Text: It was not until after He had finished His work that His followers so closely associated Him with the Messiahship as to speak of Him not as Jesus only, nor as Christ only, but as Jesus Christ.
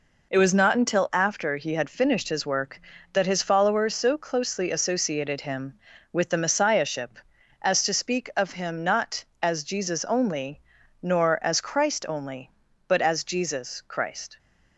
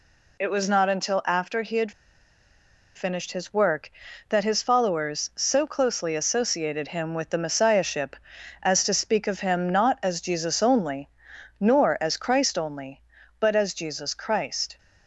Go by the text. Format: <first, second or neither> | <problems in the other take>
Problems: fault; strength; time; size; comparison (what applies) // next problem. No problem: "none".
first | pauses between "had" and "finished"; at 1.9 s; 1.0 s long